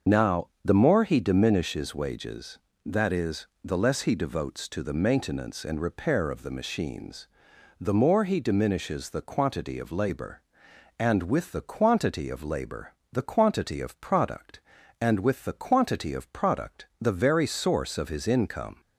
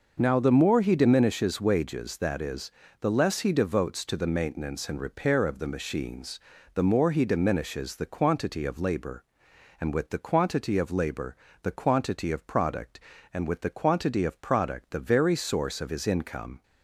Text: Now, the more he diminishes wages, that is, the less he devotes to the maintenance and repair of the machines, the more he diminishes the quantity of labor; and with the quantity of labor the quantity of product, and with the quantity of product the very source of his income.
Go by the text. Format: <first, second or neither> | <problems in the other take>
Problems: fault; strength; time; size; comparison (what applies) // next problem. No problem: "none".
second | loses the start of "Now"; at 0.0 s; 45 ms // starts louder than the rest; until 1.2 s; 6.5 dB // pauses between "labor" and "the"; slight; at 12.9 s; 0.18 s long; slight in the second